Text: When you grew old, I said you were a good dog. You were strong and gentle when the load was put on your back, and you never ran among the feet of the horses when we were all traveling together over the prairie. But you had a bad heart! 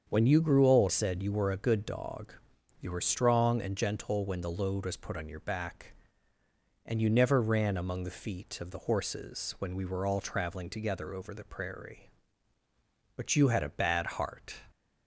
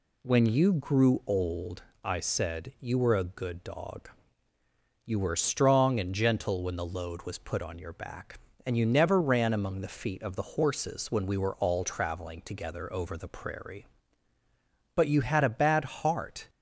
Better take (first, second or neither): second